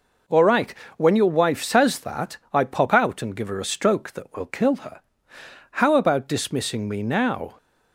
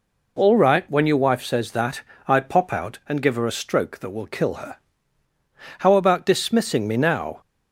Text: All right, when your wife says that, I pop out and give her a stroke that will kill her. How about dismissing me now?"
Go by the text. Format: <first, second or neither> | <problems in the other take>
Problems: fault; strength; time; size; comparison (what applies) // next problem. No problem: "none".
neither | none